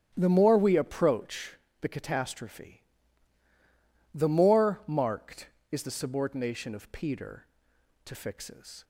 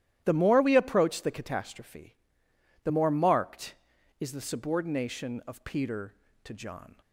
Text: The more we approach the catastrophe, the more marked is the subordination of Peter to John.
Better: second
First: starts louder than the rest; strong; until 1.1 s; 11 dB // pauses between "approach" and "the"; slight; at 1.5 s; 0.28 s long // says "Fixes" for "John"; at 8.1 s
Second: starts louder than the rest; strong; until 1.2 s; 12.5 dB

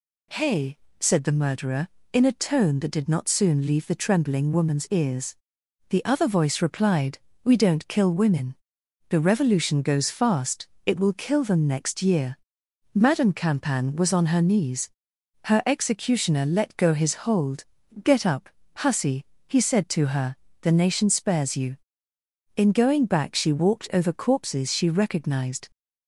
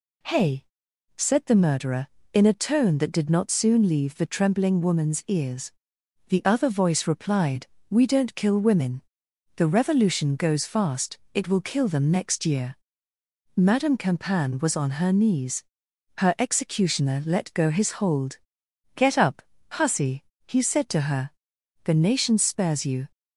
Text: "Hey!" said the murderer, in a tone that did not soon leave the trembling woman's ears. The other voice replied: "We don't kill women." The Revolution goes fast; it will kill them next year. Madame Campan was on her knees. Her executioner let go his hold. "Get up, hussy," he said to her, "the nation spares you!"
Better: second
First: goes on to say "In going back she walked over corpses she recognized"; strong; from 22.5 s on; 3.1 s long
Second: none

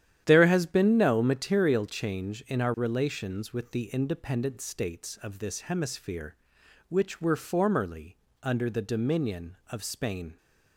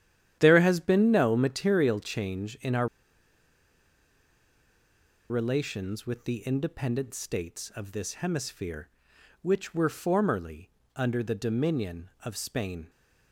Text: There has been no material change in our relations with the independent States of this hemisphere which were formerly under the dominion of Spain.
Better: first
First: starts louder than the rest; strong; until 1.2 s; 10.5 dB // pauses between "formerly" and "under"; slight; at 8.1 s; 0.26 s long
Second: starts louder than the rest; strong; until 1.4 s; 10.5 dB // pauses between "our" and "relations"; strong; at 2.8 s; 2.4 s long // pauses between "formerly" and "under"; slight; at 10.6 s; 0.26 s long

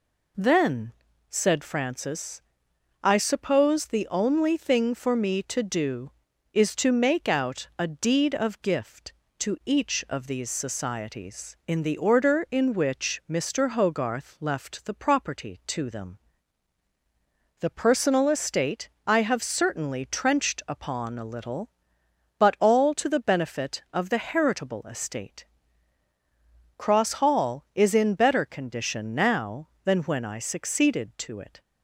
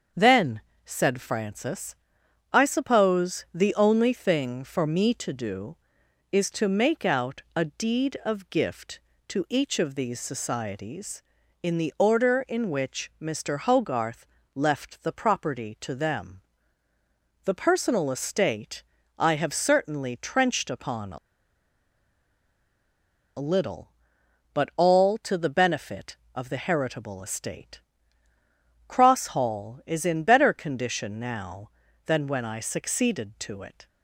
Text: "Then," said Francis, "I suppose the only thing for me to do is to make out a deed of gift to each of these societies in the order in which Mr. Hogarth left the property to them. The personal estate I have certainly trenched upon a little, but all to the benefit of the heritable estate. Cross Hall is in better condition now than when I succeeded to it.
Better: first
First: pauses between "estate" and "I"; slight; at 18.8 s; 0.16 s long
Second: starts louder than the rest; until 1.4 s; 7 dB // pauses between "Hogarth" and "left"; slight; at 14.2 s; 0.28 s long // pauses between "estate" and "I"; slight; at 18.8 s; 0.34 s long // pauses between "a" and "little"; strong; at 21.1 s; 2.2 s long

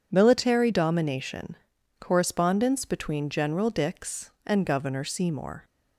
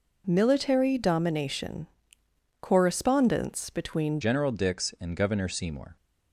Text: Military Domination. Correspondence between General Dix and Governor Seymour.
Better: first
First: none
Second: changes voice at "General"; from 4.2 s on; 1.7 s long

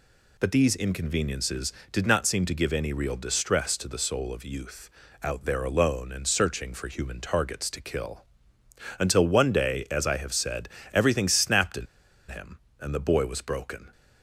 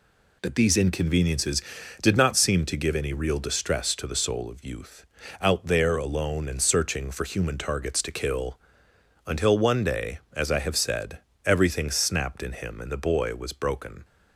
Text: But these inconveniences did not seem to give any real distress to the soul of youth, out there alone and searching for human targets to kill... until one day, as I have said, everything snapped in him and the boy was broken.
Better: second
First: pauses between "in" and "him"; at 11.8 s; 0.43 s long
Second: none

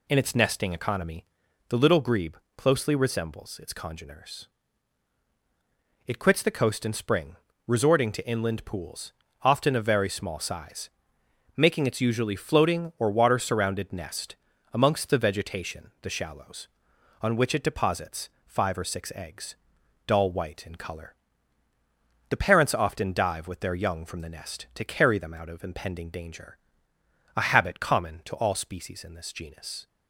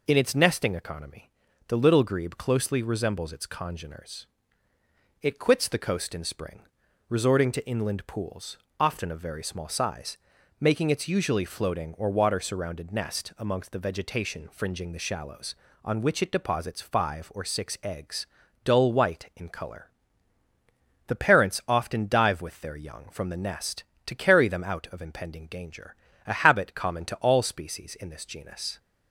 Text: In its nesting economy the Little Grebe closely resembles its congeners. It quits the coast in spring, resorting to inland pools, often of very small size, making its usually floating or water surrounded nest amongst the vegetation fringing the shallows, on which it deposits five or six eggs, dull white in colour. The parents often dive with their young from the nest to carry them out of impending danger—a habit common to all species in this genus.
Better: second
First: pauses between "economy" and "the"; at 1.2 s; 0.44 s long // pauses between "Grebe" and "closely"; slight; at 2.3 s; 0.22 s long // pauses between "nest" and "amongst"; slight; at 14.3 s; 0.36 s long // skips "fringing"; at 15.9 s // pauses between "deposits" and "five"; slight; at 18.2 s; 0.16 s long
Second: pauses between "economy" and "the"; slight; at 1.2 s; 0.36 s long

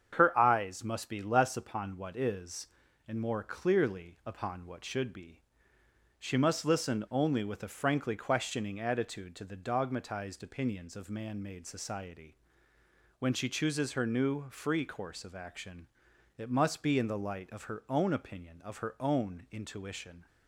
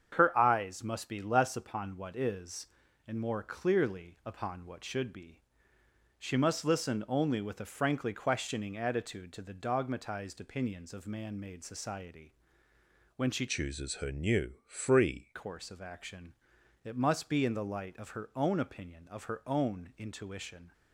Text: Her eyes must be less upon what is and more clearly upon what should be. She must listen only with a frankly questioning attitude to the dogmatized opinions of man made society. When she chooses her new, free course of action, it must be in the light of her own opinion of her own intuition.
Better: first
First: starts louder than the rest; strong; until 1.1 s; 8 dB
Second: starts louder than the rest; strong; until 1.1 s; 8 dB // changes voice from "chooses" to "free"; from 13.4 to 15.3 s; 1.9 s long

